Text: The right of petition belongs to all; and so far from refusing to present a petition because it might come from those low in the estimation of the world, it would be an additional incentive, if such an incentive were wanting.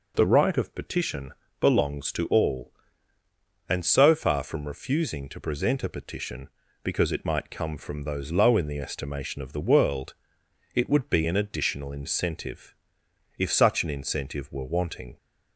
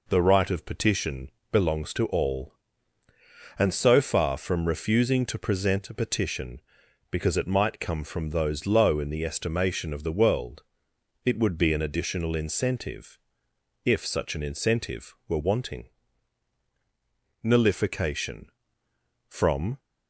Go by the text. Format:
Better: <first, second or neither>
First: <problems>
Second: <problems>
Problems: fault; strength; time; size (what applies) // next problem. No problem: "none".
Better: first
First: pauses between "petition" and "belongs"; slight; at 1.3 s; 0.26 s long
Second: pauses between "petition" and "belongs"; slight; at 1.3 s; 0.20 s long // goes on to say "NULLIFICATION From"; strong; from 17.4 s on; 2.3 s long